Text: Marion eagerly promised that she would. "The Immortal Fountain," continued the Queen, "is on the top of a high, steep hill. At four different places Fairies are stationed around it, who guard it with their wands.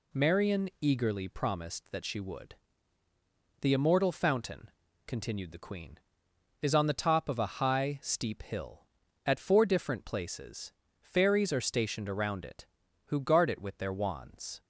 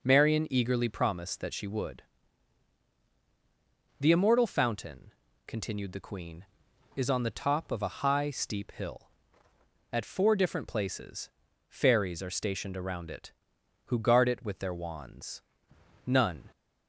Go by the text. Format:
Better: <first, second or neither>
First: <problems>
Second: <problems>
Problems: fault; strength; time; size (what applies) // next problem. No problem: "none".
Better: first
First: pauses between "places" and "Fairies"; slight; at 10.7 s; 0.26 s long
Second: pauses between "places" and "Fairies"; at 11.2 s; 0.40 s long // goes on to say "None"; slight; from 16.0 s on; 0.42 s long